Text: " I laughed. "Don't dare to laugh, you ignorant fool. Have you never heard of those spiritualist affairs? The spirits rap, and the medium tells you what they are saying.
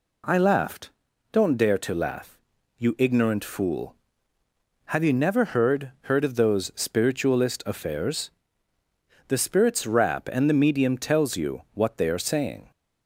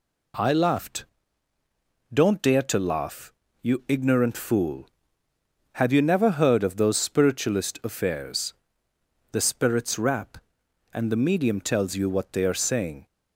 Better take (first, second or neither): second